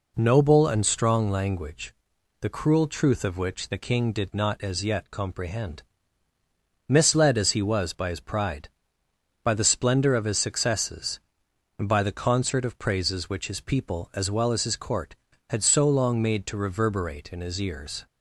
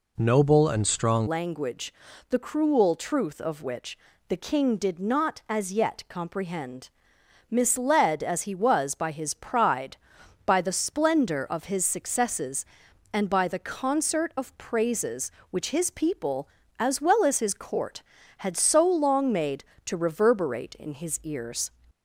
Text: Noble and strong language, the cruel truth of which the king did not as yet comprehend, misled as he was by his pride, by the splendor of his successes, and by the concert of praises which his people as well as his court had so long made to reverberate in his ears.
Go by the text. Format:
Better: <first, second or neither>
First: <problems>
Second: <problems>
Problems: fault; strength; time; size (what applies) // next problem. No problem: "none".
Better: first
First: none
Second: changes voice at "language"; from 1.2 s on; 20.5 s long // pauses between "which" and "the"; slight; at 3.9 s; 0.30 s long